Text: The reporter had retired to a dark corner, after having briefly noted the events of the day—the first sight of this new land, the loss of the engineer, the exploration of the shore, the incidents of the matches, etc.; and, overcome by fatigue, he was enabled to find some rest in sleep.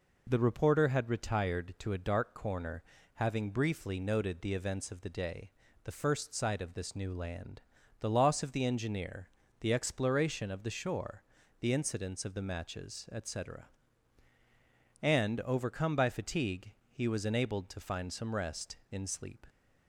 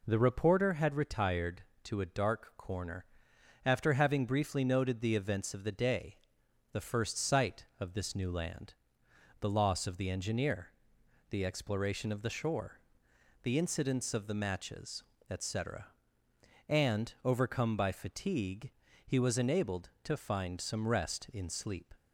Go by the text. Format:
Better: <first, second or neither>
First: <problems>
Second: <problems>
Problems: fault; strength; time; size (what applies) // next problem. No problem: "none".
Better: second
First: skips "after"; at 2.9 s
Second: none